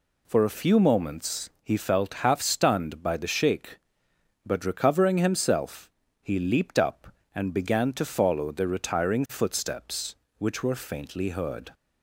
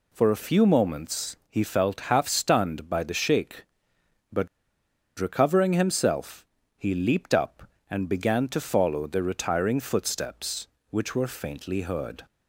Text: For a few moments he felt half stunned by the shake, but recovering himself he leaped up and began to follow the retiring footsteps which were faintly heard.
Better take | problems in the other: first | pauses between "but" and "recovering"; noticeable; at 4.4 s; 0.71 s long // pauses between "himself" and "he"; slight; at 6.4 s; 0.32 s long; slight in the first

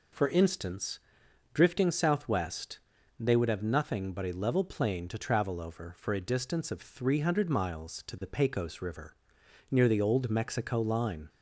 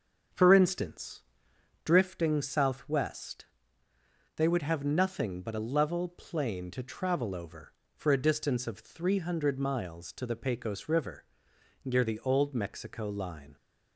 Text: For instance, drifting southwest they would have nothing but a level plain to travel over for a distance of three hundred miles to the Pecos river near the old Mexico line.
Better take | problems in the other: first | starts louder than the rest; until 1.9 s; 6.5 dB // pauses between "southwest" and "they"; noticeable; at 3.4 s; 0.92 s long; also in the first // pauses between "river" and "near"; noticeable; at 11.2 s; 0.60 s long; noticeable in the first

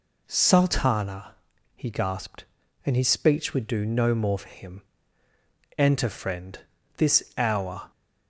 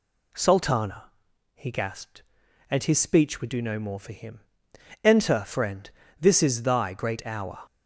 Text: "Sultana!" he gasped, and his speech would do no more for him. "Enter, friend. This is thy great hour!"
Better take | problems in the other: second | skips "is thy great"; at 7.3 s

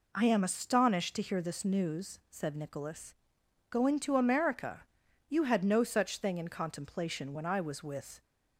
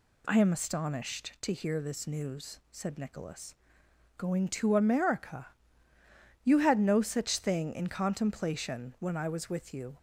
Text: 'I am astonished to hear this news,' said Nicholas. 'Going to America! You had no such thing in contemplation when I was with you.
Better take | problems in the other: second | stops before "you"; at 8.2 s

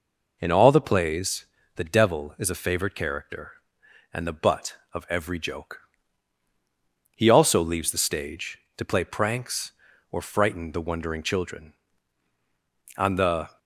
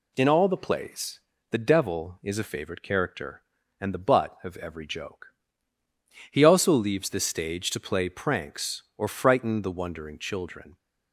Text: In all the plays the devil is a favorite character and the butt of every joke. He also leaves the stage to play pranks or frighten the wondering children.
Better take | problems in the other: second | pauses between "plays" and "the"; slight; at 1.4 s; 0.30 s long; slight in the second // goes on to say "On the"; noticeable; from 12.9 s on; 0.62 s long

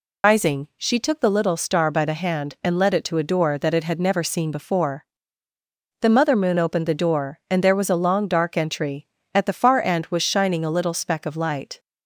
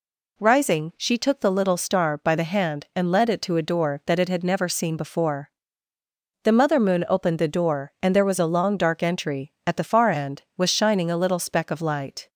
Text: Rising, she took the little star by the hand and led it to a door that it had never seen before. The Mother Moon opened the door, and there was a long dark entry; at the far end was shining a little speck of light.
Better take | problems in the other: second | loses the start of "Rising"; at 0.2 s; 105 ms

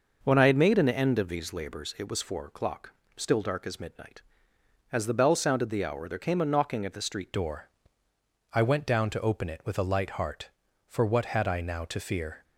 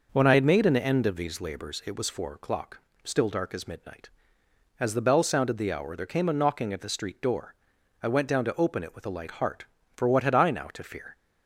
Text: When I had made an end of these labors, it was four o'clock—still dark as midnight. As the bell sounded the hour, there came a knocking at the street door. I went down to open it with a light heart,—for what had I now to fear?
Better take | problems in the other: second | changes voice at "door"; from 7.3 s on; 5.1 s long

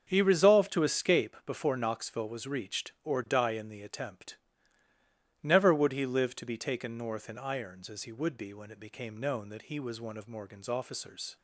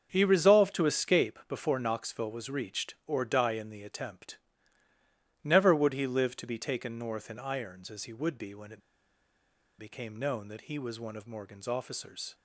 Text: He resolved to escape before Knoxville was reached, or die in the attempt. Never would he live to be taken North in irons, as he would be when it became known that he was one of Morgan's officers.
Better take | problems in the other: first | starts louder than the rest; until 1.1 s; 7 dB; also in the first // pauses between "it" and "became"; at 8.8 s; 0.98 s long

